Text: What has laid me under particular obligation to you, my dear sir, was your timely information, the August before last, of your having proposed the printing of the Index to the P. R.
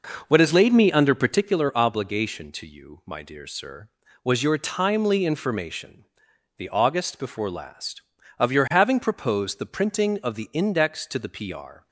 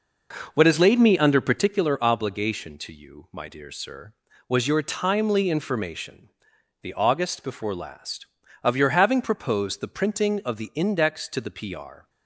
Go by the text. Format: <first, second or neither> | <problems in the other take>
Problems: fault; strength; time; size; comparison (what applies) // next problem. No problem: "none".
neither | none